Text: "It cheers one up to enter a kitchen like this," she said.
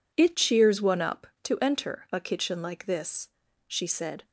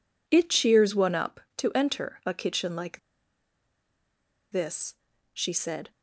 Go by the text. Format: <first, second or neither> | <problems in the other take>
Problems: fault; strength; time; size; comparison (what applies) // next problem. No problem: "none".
first | pauses between "like" and "this"; strong; at 2.9 s; 1.5 s long